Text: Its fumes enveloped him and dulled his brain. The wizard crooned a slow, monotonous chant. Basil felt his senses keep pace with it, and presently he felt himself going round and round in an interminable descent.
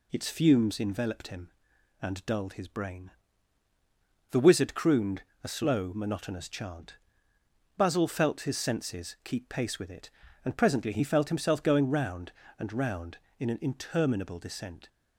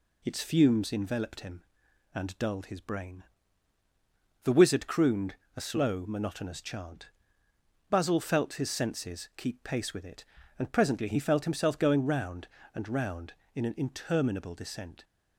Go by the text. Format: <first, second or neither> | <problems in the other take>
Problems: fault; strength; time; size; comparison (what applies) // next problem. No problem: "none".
neither | pauses between "crooned" and "a"; slight; the same in both